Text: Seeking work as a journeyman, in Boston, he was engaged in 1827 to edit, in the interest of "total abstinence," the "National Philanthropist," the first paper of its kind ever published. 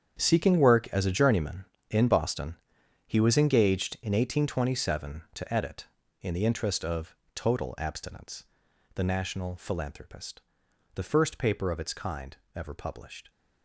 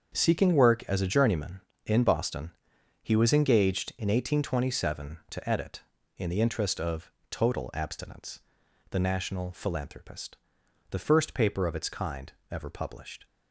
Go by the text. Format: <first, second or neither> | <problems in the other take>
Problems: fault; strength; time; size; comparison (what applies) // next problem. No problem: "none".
second | gets quieter; strong; throughout; 13.5 dB // starts louder than the rest; strong; until 1.2 s; 8.5 dB; strong in the second // pauses between "of" and "total"; slight; at 7.1 s; 0.22 s long; slight in the second // pauses between "kind" and "ever"; slight; at 12.3 s; 0.20 s long; slight in the second